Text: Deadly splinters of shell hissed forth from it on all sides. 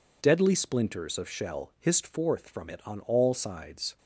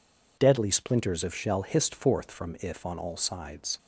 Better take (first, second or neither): first